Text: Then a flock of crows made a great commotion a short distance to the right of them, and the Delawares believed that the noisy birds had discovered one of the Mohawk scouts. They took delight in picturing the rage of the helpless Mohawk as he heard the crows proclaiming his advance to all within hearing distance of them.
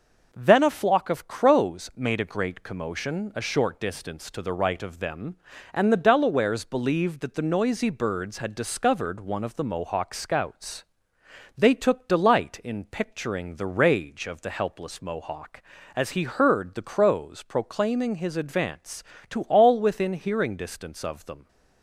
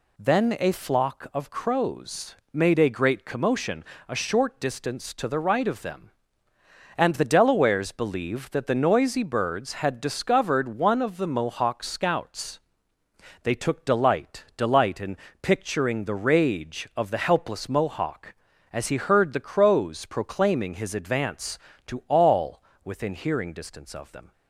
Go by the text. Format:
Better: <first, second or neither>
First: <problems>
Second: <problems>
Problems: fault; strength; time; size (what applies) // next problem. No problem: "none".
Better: first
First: none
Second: pauses between "crows" and "made"; slight; at 2.3 s; 0.16 s long // pauses between "commotion" and "a"; slight; at 3.8 s; 0.24 s long // says "delight" twice; at 14.5 s // pauses between "in" and "picturing"; slight; at 15.1 s; 0.24 s long // pauses between "all" and "within"; slight; at 22.6 s; 0.22 s long